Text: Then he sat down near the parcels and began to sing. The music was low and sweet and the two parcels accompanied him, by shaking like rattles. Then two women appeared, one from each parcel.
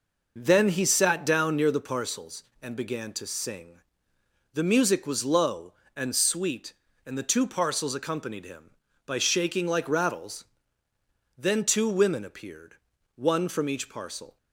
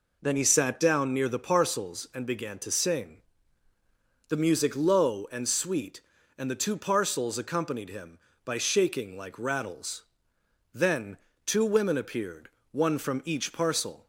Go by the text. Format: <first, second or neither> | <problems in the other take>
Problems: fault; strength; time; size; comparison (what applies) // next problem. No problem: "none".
first | skips "was"; at 4.7 s // pauses between "Then" and "two"; slight; at 11.1 s; 0.30 s long